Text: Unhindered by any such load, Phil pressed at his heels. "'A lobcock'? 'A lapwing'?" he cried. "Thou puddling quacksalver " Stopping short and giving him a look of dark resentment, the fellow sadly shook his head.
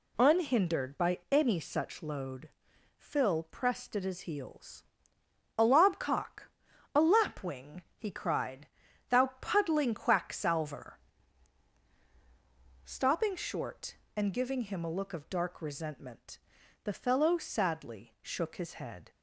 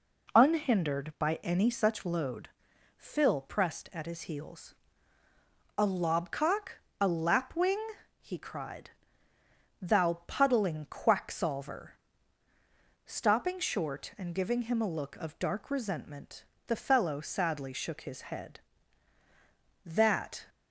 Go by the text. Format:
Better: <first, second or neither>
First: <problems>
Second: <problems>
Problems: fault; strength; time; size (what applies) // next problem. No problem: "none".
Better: first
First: none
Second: goes on to say "That"; noticeable; from 19.8 s on; 0.64 s long